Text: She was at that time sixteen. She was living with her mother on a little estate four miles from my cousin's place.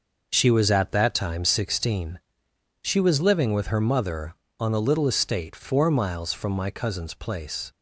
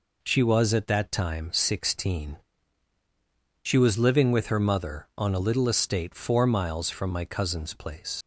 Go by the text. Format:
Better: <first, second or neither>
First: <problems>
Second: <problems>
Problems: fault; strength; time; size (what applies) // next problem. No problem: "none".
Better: first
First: none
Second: leaves "place" unfinished; at 8.2 s; 70 ms